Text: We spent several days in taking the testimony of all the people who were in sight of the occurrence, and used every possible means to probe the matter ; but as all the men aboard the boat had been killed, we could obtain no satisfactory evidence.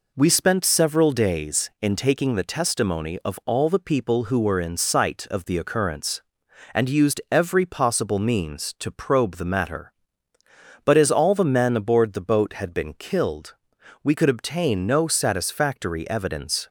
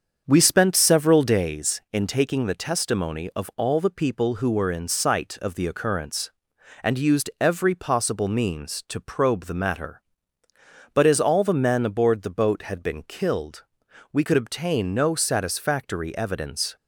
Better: first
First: none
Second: starts louder than the rest; strong; until 1.4 s; 7 dB

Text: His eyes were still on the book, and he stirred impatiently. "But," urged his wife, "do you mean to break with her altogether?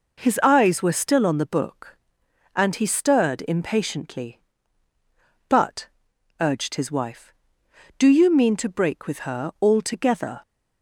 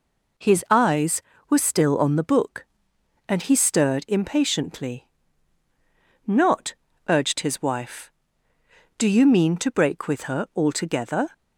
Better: first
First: none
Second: says "Not" for "But"; at 6.2 s

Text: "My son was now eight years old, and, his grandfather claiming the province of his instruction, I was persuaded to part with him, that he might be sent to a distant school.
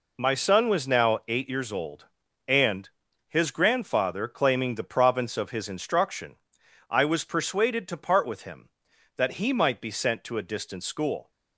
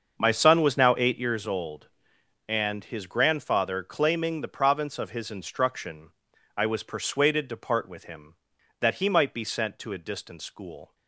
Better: first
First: none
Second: starts louder than the rest; until 1.4 s; 6.5 dB

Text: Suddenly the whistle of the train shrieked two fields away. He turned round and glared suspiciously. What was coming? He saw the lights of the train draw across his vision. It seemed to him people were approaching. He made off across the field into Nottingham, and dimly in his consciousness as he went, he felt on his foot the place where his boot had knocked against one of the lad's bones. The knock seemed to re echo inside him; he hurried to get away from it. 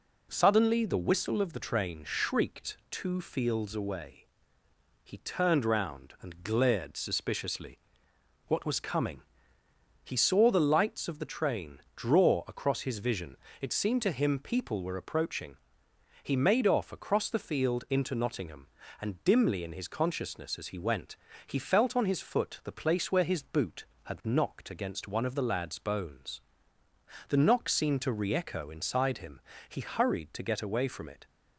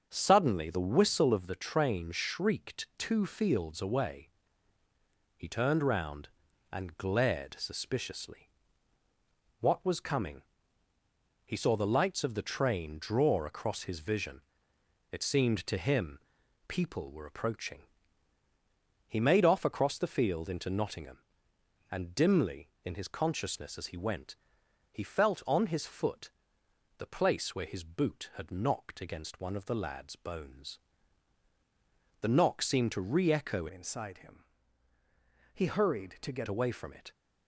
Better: first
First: none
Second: starts louder than the rest; until 1.1 s; 6.5 dB // pauses between "him" and "people"; noticeable; at 16.1 s; 0.50 s long // pauses between "foot" and "the"; noticeable; at 26.3 s; 0.68 s long // changes voice from "inside" to "get"; from 33.6 to 36.4 s; 2.8 s long

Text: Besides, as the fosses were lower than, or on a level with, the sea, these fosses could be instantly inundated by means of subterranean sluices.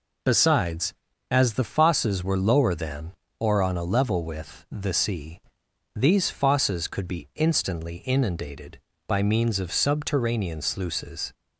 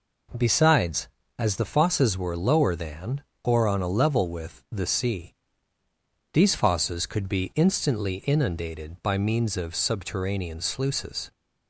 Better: neither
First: none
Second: none

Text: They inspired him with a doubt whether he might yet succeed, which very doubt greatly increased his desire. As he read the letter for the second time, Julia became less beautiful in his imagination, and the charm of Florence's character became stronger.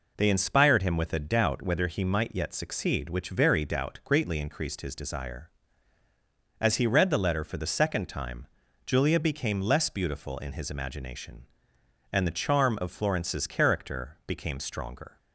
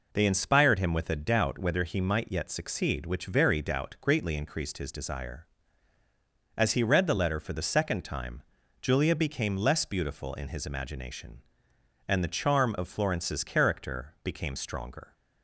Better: neither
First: none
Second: none

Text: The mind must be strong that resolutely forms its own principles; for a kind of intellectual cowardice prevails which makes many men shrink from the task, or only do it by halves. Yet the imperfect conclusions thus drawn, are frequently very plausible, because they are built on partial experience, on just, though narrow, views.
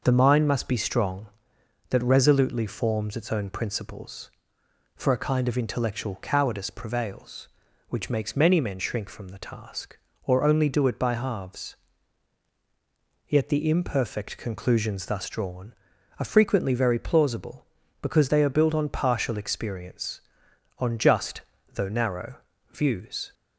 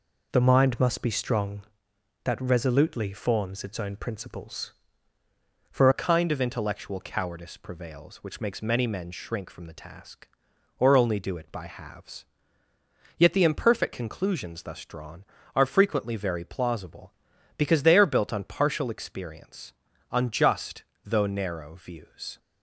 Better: first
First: none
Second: changes voice at "a"; from 5.9 s on; 16.4 s long

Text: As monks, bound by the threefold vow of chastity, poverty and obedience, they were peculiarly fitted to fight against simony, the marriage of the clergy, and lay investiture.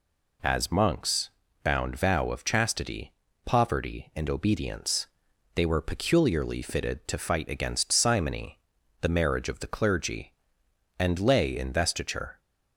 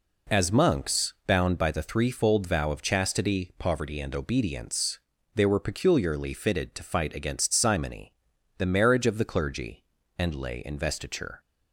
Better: second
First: skips "by the threefold"; at 1.9 s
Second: none

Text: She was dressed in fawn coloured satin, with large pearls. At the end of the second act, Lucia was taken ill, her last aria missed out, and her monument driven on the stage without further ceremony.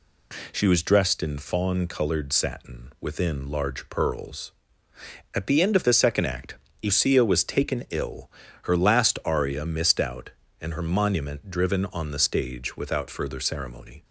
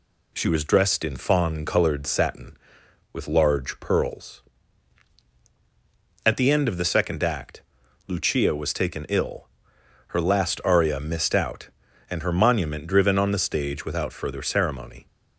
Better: second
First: says "within" for "with"; at 3.0 s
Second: none

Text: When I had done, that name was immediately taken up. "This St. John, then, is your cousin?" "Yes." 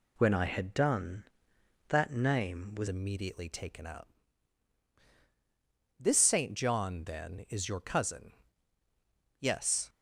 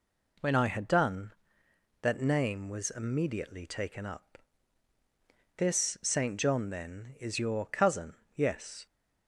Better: second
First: changes voice at "immediately"; from 2.8 s on; 7.0 s long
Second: none

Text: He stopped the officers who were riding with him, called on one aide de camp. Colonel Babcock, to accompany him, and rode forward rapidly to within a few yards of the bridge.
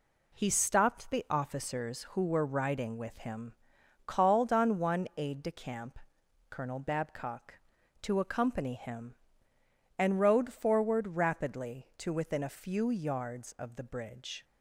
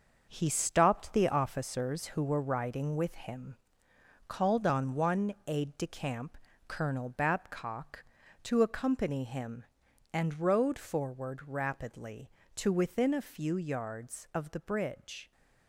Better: first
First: none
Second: gets quieter; strong; throughout; 8 dB

